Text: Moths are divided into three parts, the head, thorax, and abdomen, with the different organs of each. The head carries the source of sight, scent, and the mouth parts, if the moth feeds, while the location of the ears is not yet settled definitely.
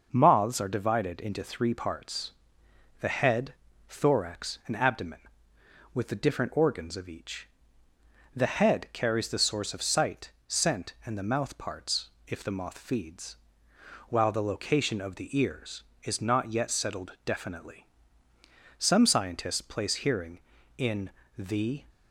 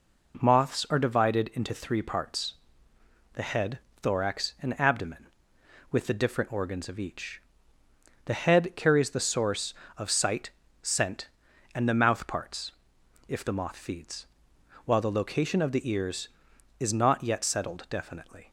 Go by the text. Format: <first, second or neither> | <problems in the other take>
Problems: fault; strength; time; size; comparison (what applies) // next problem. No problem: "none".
second | goes on to say "Some scientists place hearing in the"; strong; from 18.7 s on; 3.0 s long